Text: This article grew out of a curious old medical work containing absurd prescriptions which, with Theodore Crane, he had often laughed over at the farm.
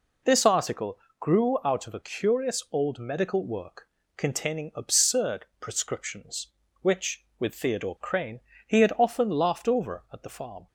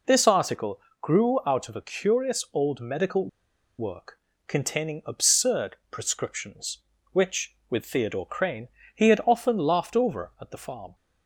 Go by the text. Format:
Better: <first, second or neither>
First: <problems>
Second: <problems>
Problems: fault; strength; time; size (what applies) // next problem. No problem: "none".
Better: first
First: pauses between "article" and "grew"; slight; at 0.9 s; 0.22 s long // pauses between "work" and "containing"; slight; at 3.8 s; 0.28 s long // pauses between "absurd" and "prescriptions"; slight; at 5.4 s; 0.16 s long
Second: pauses between "article" and "grew"; slight; at 0.7 s; 0.22 s long // pauses between "medical" and "work"; noticeable; at 3.2 s; 0.50 s long // pauses between "work" and "containing"; slight; at 4.1 s; 0.28 s long // pauses between "absurd" and "prescriptions"; slight; at 5.7 s; 0.16 s long